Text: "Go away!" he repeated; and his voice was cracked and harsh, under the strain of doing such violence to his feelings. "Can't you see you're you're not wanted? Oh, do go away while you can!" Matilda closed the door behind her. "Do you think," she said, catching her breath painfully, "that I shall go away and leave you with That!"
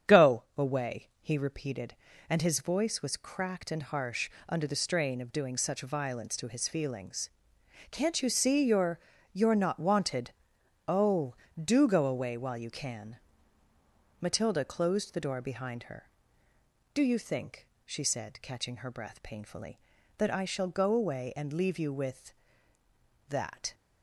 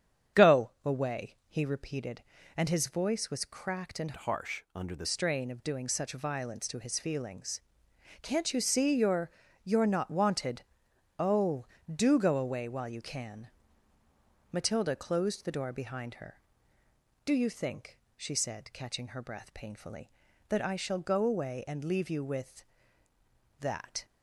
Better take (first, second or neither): first